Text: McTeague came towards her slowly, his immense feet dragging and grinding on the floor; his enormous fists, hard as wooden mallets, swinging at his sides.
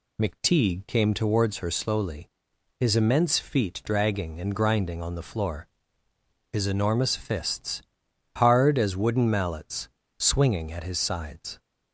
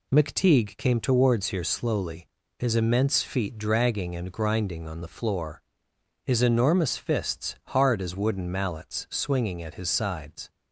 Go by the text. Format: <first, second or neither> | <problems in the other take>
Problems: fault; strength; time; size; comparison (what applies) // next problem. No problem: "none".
first | says "here" for "her"; at 1.4 s